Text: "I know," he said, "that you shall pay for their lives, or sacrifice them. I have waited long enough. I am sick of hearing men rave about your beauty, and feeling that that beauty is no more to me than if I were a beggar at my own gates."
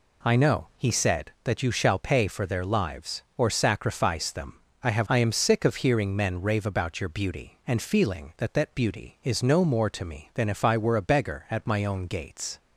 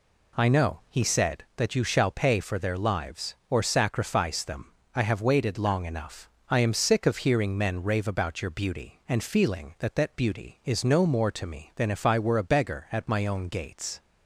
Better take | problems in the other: second | skips "waited long enough"; at 5.0 s

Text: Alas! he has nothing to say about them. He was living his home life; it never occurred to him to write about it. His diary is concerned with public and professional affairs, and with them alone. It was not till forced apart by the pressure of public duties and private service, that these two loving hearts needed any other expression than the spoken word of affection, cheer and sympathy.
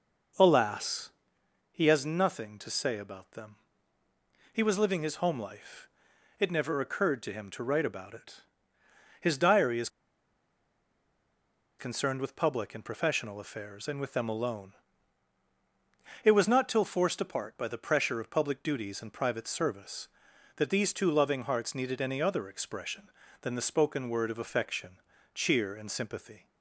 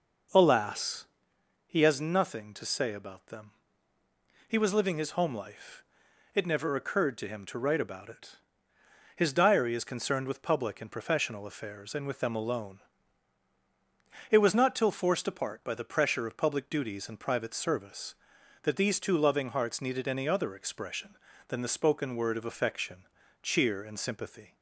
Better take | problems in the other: second | pauses between "is" and "concerned"; strong; at 9.8 s; 1.9 s long

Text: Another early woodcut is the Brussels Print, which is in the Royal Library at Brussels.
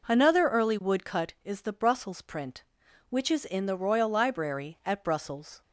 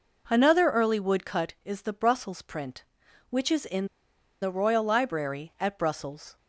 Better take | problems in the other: first | pauses between "in" and "the"; noticeable; at 3.8 s; 0.55 s long

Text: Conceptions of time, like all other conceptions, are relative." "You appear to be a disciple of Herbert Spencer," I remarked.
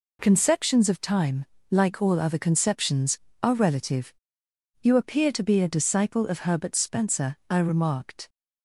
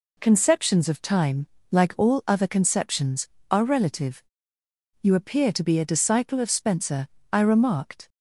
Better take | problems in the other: first | skips "Herbert"; at 6.4 s

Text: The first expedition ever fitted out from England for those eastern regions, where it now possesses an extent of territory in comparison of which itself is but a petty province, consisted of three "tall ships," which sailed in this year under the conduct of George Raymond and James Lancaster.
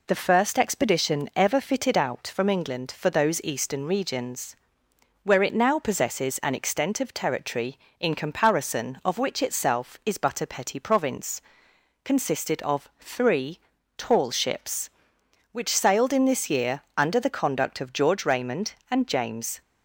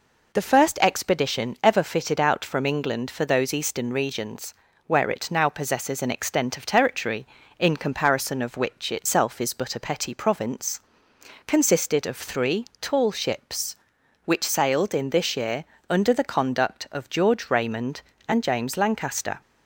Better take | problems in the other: second | pauses between "three" and "tall"; at 13.5 s; 0.38 s long; slight in the second // pauses between "year" and "under"; slight; at 16.8 s; 0.18 s long; slight in the second // stops before "Lancaster"; at 19.6 s

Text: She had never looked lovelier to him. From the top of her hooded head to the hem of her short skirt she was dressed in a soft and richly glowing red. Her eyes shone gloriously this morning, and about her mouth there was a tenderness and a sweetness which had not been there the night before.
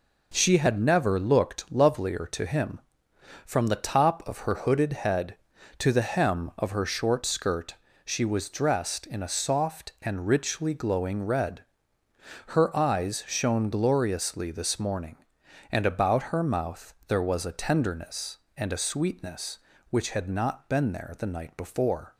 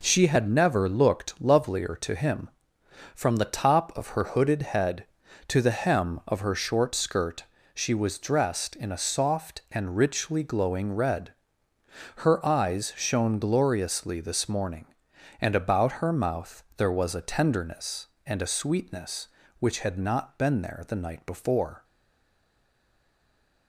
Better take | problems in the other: first | pauses between "skirt" and "she"; slight; at 7.4 s; 0.32 s long; slight in the first // stays silent after the last word; noticeable; from 21.8 s on; 1.8 s long

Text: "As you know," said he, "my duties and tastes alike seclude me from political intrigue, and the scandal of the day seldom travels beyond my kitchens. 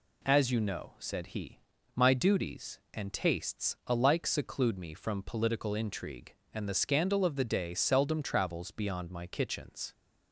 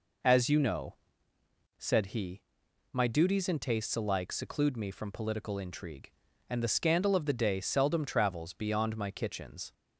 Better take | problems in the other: neither | none

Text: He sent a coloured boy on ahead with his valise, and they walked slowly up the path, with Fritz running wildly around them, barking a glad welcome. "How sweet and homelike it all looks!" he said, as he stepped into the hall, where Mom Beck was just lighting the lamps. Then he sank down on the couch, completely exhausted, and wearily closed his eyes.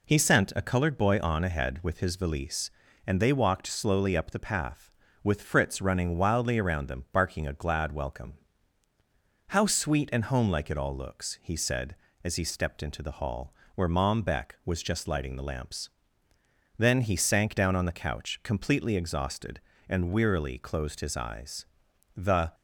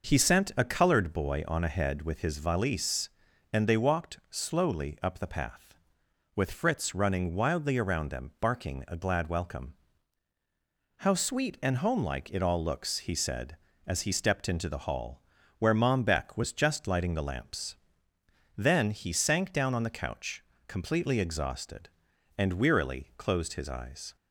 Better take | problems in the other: second | goes on to say "The"; slight; from 22.1 s on; 0.38 s long

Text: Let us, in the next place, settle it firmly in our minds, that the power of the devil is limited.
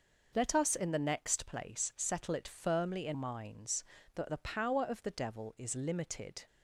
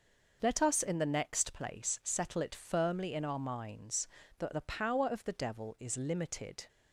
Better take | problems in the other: second | skips "our"; at 3.1 s

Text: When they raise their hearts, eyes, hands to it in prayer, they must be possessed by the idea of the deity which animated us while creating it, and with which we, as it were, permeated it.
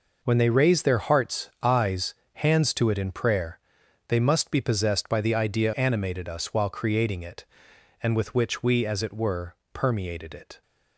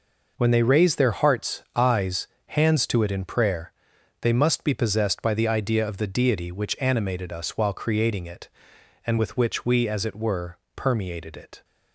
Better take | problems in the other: second | skips "of the deity which"; at 5.7 s

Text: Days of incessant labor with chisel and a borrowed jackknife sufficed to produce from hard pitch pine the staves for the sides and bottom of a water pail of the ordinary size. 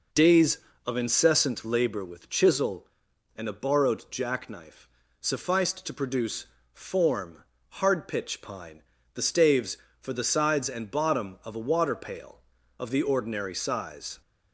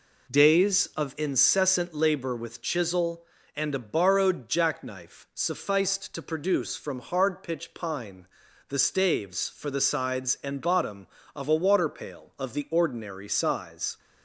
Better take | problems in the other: second | pauses between "jackknife" and "sufficed"; slight; at 4.8 s; 0.32 s long // says "form" for "from"; at 6.7 s // pauses between "pine" and "the"; slight; at 8.8 s; 0.34 s long; also in the second

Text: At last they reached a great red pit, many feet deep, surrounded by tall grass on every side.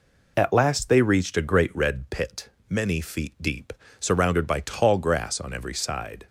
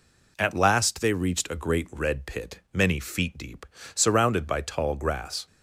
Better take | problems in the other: first | stops before "on every side"; at 5.4 s

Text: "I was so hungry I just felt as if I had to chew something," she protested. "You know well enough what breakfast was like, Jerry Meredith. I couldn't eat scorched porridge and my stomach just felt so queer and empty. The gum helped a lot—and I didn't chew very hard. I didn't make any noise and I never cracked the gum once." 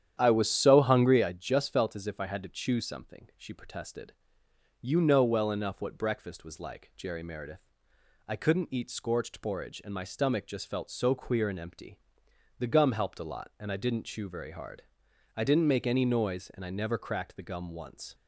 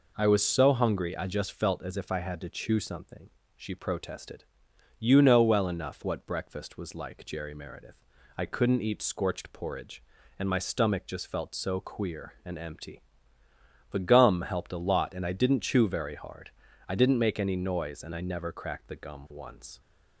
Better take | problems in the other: second | starts louder than the rest; strong; until 1.4 s; 10 dB

